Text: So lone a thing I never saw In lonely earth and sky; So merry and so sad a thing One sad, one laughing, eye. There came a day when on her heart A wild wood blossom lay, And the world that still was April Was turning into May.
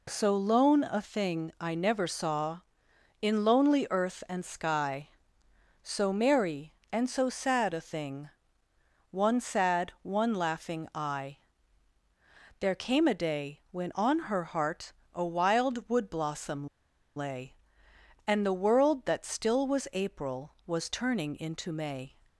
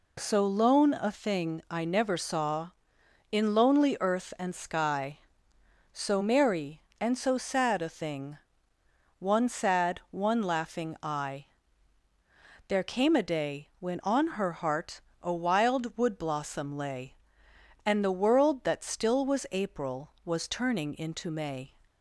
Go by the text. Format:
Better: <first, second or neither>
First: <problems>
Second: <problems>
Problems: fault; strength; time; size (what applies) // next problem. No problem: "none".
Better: second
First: pauses between "thing" and "One"; noticeable; at 8.3 s; 0.80 s long // pauses between "heart" and "A"; slight; at 14.9 s; 0.20 s long // pauses between "blossom" and "lay"; noticeable; at 16.6 s; 0.50 s long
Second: pauses between "thing" and "One"; noticeable; at 8.3 s; 0.80 s long // pauses between "heart" and "A"; slight; at 15.0 s; 0.20 s long